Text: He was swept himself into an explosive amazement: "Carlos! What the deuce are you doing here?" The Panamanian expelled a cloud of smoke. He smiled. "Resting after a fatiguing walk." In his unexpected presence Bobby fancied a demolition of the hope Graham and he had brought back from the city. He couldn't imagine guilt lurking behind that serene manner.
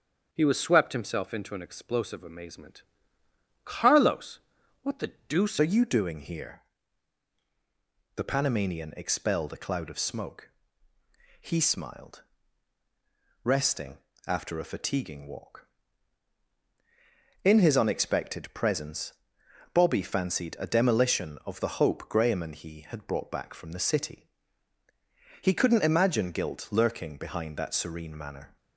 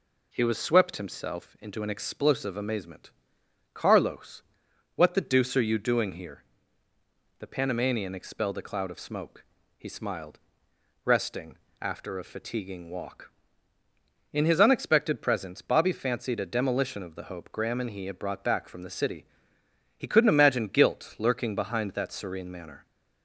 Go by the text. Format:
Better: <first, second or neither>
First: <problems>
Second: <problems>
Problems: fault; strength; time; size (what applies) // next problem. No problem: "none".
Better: second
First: starts louder than the rest; until 1.3 s; 7 dB // pauses between "the" and "deuce"; slight; at 5.1 s; 0.16 s long // changes voice at "are"; from 5.5 s on; 23.0 s long // pauses between "Resting" and "after"; slight; at 13.9 s; 0.28 s long // pauses between "presence" and "Bobby"; noticeable; at 19.1 s; 0.58 s long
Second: pauses between "Resting" and "after"; slight; at 11.5 s; 0.24 s long